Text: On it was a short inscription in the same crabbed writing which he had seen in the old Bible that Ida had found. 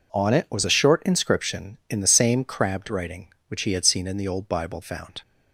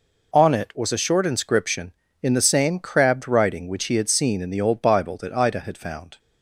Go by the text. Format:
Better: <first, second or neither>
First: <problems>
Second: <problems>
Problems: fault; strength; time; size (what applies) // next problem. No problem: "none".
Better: second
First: skips "that Ida had"; at 4.8 s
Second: none